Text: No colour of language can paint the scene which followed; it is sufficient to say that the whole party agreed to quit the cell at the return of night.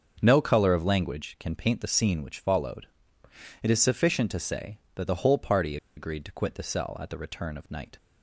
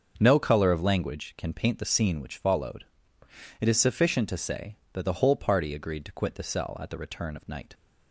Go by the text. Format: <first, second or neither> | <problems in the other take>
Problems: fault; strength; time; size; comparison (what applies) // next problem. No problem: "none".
second | starts louder than the rest; until 1.2 s; 6.5 dB; also in the second // pauses between "party" and "agreed"; slight; at 5.7 s; 0.20 s long